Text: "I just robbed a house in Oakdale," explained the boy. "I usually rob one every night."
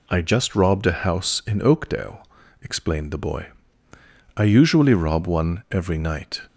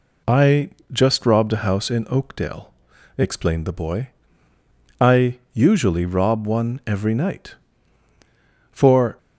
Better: first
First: none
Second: pauses between "I" and "just"; slight; at 0.6 s; 0.22 s long // goes on to say "For"; slight; from 8.7 s on; 0.46 s long

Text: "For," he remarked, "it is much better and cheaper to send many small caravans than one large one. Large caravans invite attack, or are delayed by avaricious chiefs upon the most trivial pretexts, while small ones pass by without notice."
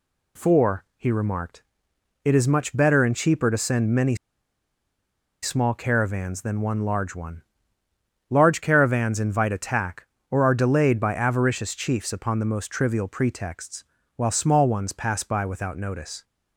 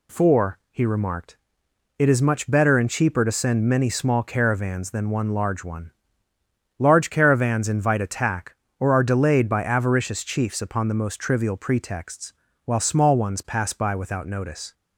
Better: second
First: pauses between "many" and "small"; strong; at 4.1 s; 1.2 s long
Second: none

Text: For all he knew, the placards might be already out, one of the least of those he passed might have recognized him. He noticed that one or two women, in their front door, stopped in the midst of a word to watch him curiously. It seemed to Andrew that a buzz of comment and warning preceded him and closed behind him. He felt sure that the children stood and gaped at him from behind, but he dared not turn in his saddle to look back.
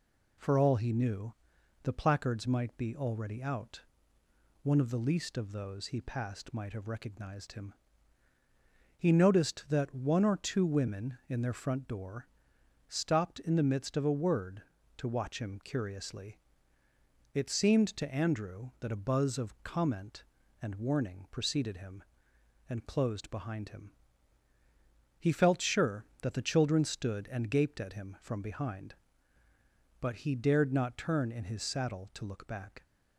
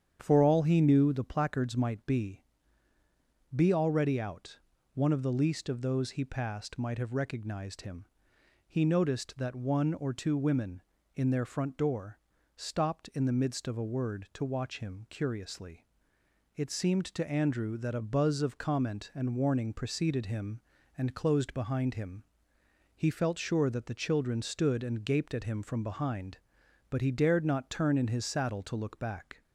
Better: first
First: none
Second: starts louder than the rest; strong; until 1.2 s; 8.5 dB // says "be" twice; at 3.5 s

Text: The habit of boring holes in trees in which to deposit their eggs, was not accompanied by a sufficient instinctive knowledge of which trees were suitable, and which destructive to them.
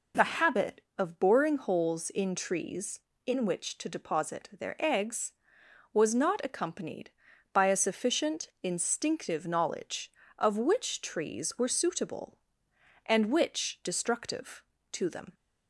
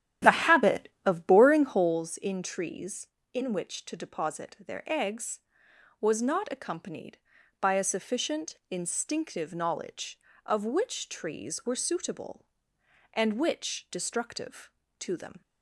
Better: first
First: pauses between "sufficient" and "instinctive"; slight; at 8.4 s; 0.16 s long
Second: starts louder than the rest; strong; until 2.1 s; 10.5 dB // pauses between "sufficient" and "instinctive"; slight; at 8.5 s; 0.16 s long

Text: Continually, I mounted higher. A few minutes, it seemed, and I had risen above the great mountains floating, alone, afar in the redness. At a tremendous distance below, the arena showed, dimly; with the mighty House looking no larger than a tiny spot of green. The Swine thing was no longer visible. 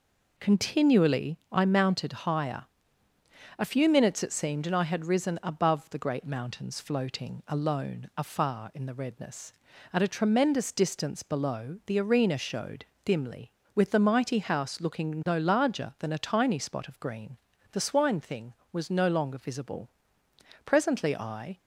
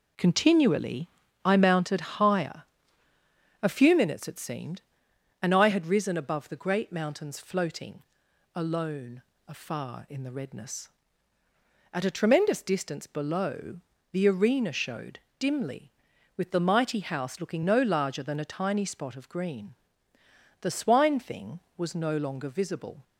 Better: second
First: goes on to say "Presently I"; noticeable; from 20.6 s on; 0.92 s long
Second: none

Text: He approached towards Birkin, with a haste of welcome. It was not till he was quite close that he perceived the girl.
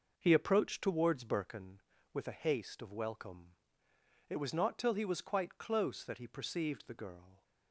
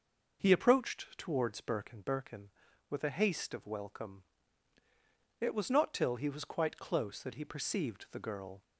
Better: first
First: none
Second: says "Birkin" twice; at 2.0 s

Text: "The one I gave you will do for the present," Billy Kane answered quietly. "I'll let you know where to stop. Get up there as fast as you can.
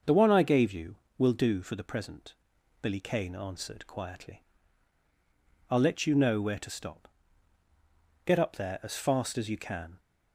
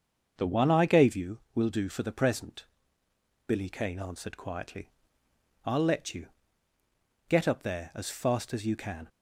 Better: first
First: starts louder than the rest; until 1.2 s; 6.5 dB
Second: starts louder than the rest; until 1.3 s; 6.5 dB // skips "know where to stop"; at 6.7 s

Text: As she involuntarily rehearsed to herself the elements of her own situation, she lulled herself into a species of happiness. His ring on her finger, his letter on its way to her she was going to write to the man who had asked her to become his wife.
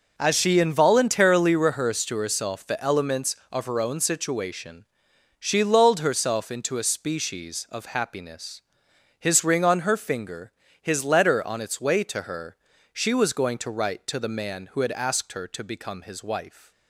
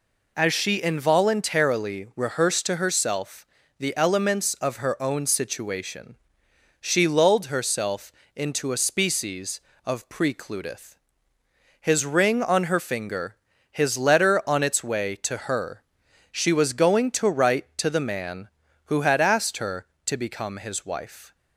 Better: first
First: pauses between "her" and "she"; at 12.5 s; 0.40 s long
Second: pauses between "herself" and "the"; slight; at 3.4 s; 0.32 s long // pauses between "herself" and "into"; slight; at 8.1 s; 0.24 s long // says "precludeth" for "happiness"; at 10.0 s // pauses between "her" and "she"; noticeable; at 15.8 s; 0.54 s long

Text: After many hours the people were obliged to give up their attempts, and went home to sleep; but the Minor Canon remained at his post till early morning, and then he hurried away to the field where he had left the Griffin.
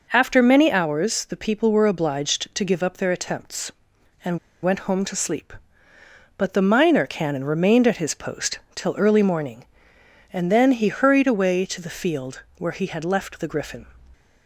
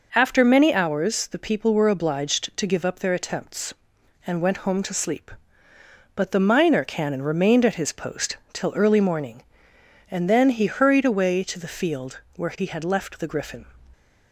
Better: second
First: pauses between "and" and "went"; slight; at 4.3 s; 0.24 s long // pauses between "post" and "till"; slight; at 8.6 s; 0.16 s long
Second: pauses between "post" and "till"; slight; at 8.3 s; 0.16 s long

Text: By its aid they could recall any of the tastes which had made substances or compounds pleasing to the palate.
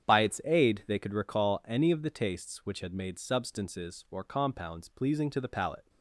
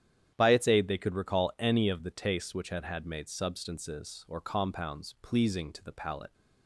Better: first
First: starts louder than the rest; strong; until 1.1 s; 8.5 dB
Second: starts louder than the rest; strong; until 1.3 s; 10 dB // says "had" twice; at 2.8 s

